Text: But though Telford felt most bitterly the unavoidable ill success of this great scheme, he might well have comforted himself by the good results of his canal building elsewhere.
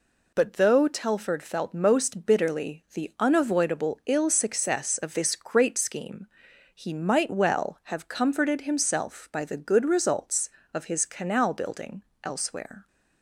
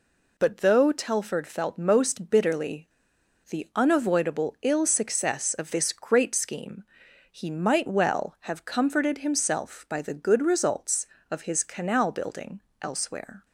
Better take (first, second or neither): first